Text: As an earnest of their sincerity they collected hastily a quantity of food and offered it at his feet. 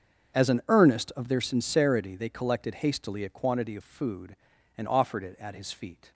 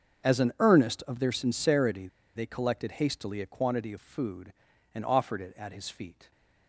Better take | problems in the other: first | starts louder than the rest; until 1.3 s; 6.5 dB; also in the first // pauses between "sincerity" and "they"; slight; at 2.0 s; 0.28 s long

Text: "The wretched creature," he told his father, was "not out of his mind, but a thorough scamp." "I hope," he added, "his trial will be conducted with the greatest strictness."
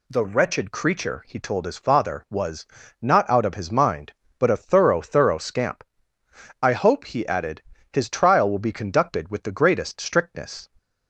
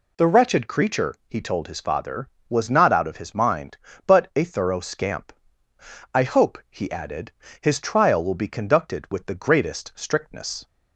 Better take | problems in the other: second | pauses between "was" and "not"; slight; at 2.6 s; 0.34 s long // says "thorough" twice; at 5.0 s

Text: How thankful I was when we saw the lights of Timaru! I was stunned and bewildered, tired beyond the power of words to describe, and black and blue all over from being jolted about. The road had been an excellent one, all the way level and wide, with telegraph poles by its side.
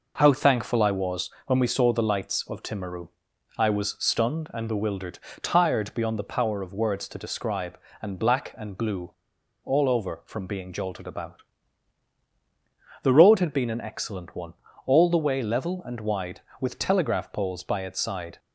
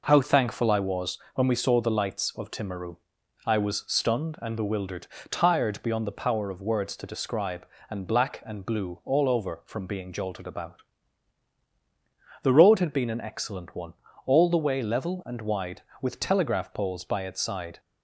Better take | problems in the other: second | pauses between "was" and "when"; slight; at 1.2 s; 0.16 s long; slight in the second // pauses between "blue" and "all"; noticeable; at 9.1 s; 0.52 s long

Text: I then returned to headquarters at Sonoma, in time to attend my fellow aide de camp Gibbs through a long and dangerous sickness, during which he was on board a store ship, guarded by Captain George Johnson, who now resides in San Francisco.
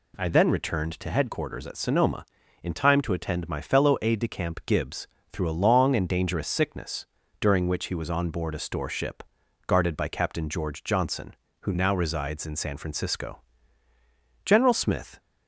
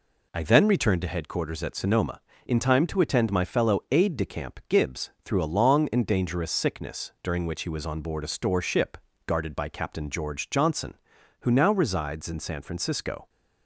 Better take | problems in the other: second | pauses between "Gibbs" and "through"; slight; at 5.0 s; 0.24 s long; slight in the second // goes on to say "General Smith"; noticeable; from 14.4 s on; 0.74 s long

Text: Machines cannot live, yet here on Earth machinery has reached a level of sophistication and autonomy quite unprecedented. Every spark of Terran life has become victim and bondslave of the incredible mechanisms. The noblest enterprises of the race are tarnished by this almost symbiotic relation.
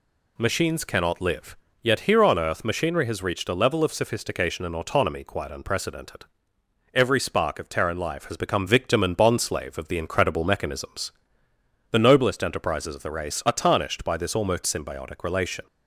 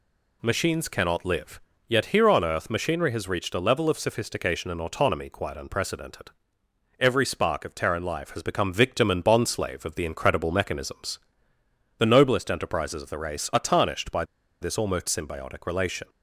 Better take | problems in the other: first | pauses between "by" and "this"; at 14.2 s; 0.37 s long

